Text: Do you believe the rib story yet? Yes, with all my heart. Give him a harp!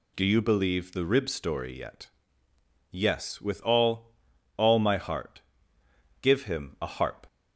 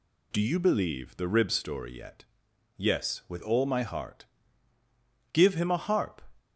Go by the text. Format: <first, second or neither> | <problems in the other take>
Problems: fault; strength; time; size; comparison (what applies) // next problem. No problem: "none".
second | says "all" twice; at 4.5 s